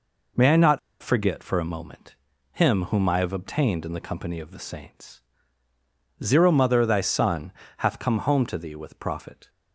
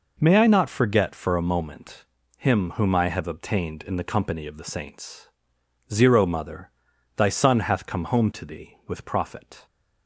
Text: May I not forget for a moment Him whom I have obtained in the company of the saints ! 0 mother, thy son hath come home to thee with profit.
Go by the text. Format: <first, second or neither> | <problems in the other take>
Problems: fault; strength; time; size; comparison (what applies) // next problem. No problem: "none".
second | pauses between "not" and "forget"; slight; at 0.7 s; 0.23 s long // pauses between "moment" and "Him"; at 2.1 s; 0.38 s long; slight in the second // pauses between "son" and "hath"; slight; at 7.5 s; 0.26 s long